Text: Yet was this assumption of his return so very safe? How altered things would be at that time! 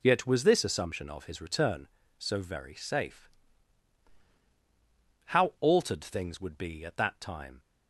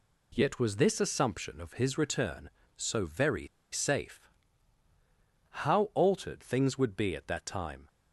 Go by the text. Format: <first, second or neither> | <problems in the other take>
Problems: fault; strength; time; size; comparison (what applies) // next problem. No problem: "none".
first | pauses between "very" and "safe"; slight; at 3.4 s; 0.27 s long